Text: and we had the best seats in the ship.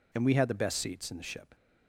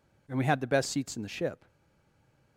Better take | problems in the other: first | stays silent after the last word; slight; from 1.6 s on; 0.9 s long

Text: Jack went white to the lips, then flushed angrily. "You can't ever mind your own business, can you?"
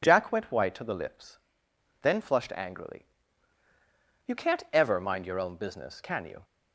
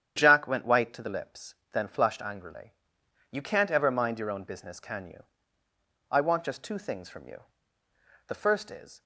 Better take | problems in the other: first | starts louder than the rest; strong; until 1.1 s; 9 dB // goes on to say "I want just two things from you The first is"; strong; from 6.1 s on; 2.9 s long

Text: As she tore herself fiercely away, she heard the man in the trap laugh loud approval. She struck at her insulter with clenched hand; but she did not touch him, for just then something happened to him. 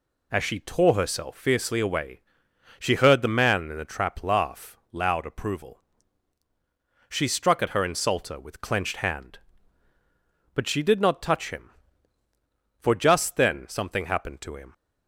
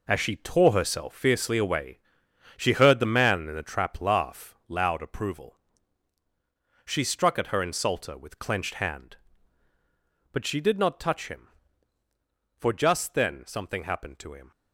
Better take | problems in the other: first | gets quieter; strong; throughout; 9.5 dB

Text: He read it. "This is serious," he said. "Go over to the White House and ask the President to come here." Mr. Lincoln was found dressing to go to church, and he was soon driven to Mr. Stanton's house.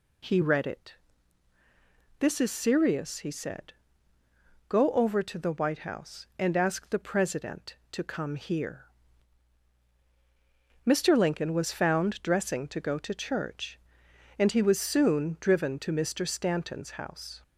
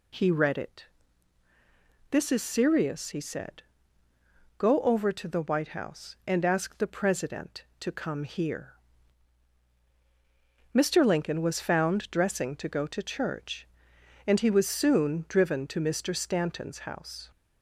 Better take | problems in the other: neither | none

